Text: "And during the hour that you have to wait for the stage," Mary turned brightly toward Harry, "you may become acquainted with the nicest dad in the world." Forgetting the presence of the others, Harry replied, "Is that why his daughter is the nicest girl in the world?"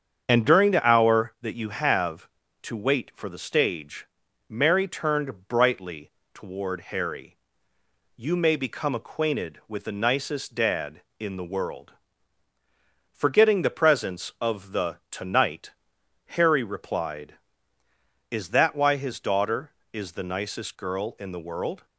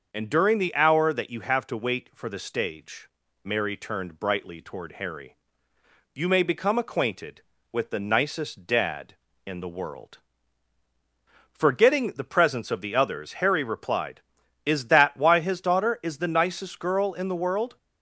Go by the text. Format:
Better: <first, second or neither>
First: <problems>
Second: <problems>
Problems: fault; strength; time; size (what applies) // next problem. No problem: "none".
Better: second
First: starts louder than the rest; strong; until 1.2 s; 7.5 dB // pauses between "brightly" and "toward"; slight; at 6.1 s; 0.22 s long // says "tonight" for "others"; at 15.1 s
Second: starts louder than the rest; until 1.1 s; 6.5 dB